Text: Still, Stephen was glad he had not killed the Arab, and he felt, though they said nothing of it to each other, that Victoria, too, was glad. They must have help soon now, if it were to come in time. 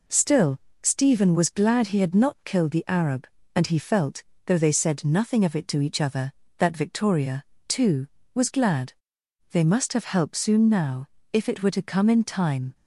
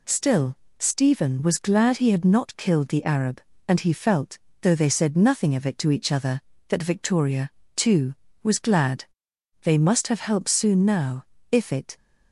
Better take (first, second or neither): first